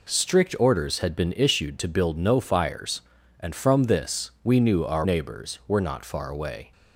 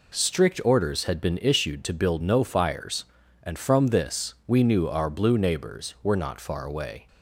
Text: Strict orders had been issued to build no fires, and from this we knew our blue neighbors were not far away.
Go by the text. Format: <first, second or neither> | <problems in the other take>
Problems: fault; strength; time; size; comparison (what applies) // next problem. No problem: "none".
second | skips "blue"; at 5.0 s